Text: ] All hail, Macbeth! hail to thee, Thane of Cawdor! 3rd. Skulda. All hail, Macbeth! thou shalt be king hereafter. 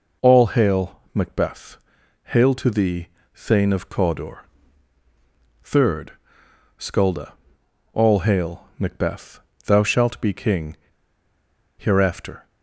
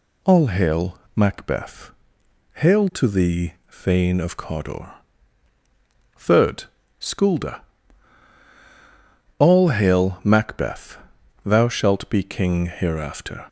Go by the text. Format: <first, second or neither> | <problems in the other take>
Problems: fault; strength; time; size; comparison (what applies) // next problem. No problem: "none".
second | pauses between "king" and "hereafter"; at 10.7 s; 0.99 s long